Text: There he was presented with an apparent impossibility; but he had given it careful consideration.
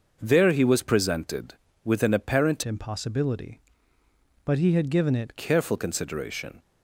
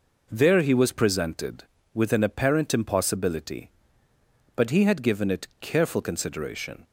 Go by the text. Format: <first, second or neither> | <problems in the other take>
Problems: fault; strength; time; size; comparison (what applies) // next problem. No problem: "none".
second | starts louder than the rest; noticeable; until 1.2 s; 6 dB // changes voice from "impossibility" to "it"; from 2.6 to 5.3 s; 2.7 s long